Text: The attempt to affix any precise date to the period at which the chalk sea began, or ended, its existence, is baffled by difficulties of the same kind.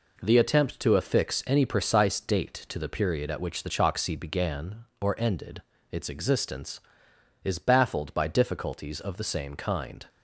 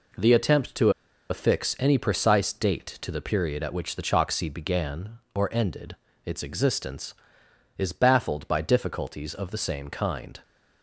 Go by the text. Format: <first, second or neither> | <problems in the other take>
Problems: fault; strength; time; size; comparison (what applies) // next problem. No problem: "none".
first | pauses between "to" and "affix"; at 0.9 s; 0.39 s long